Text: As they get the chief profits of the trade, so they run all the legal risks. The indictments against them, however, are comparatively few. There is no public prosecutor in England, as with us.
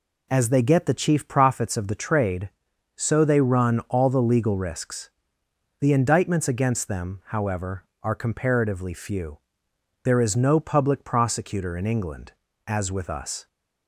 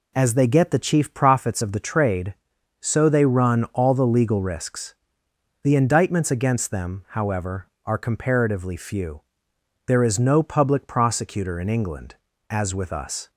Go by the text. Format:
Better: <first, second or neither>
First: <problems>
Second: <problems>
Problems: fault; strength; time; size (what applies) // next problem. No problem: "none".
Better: neither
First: none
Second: none